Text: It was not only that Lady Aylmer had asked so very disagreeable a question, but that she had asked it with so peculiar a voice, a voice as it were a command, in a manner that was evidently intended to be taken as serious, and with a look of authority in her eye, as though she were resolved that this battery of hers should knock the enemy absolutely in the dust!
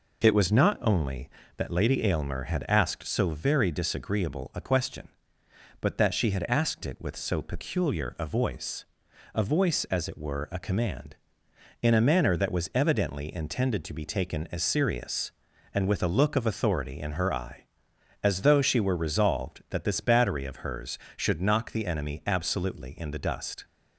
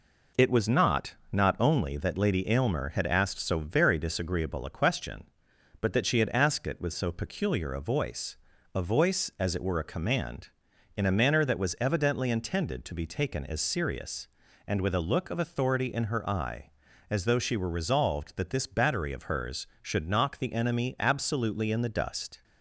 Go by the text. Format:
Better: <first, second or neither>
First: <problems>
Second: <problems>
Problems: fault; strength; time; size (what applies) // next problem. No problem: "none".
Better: first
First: none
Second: says "not" twice; at 1.3 s